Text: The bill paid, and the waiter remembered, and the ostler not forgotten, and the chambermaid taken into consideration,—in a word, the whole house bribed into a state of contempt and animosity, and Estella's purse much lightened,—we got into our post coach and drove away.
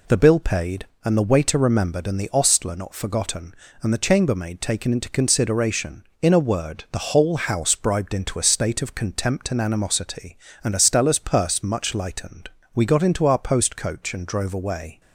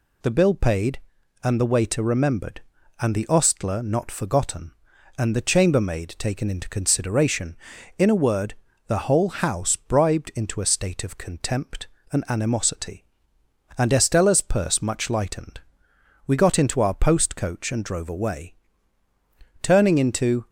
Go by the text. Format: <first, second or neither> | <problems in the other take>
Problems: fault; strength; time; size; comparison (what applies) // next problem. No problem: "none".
first | goes on to say "Turning into"; noticeable; from 19.6 s on; 0.86 s long